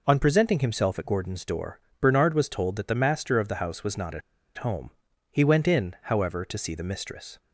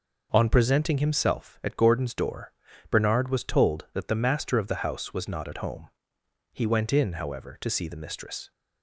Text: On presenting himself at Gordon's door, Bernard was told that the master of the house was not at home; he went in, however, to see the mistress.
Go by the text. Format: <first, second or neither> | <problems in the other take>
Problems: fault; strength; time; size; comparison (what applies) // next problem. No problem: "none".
second | pauses between "at" and "home"; at 4.2 s; 0.37 s long